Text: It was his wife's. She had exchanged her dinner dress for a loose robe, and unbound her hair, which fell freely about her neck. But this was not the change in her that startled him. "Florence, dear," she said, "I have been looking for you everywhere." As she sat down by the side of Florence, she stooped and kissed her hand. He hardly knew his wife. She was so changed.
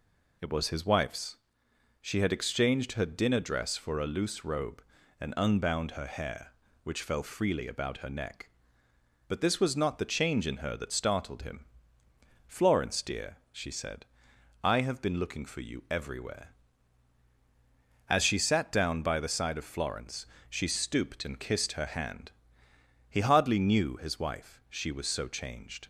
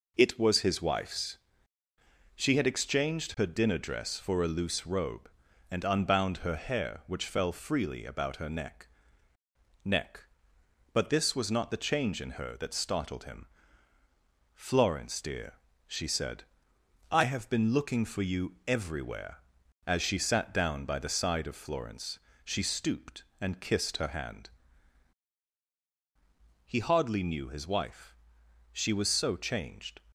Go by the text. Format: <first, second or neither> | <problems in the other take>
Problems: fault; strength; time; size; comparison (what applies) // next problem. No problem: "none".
first | says "neck" twice; at 9.8 s